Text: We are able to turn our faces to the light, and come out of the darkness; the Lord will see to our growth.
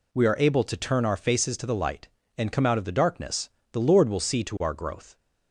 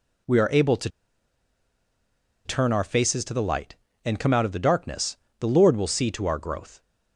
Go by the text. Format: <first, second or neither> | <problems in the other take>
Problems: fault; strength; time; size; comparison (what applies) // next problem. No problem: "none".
first | pauses between "to" and "turn"; strong; at 0.8 s; 1.5 s long